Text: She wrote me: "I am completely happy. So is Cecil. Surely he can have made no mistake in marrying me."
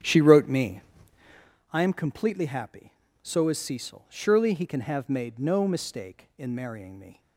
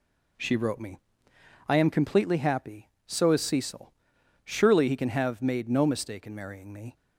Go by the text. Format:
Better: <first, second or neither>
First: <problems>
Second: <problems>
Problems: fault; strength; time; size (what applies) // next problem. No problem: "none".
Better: second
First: starts louder than the rest; strong; until 1.5 s; 9 dB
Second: none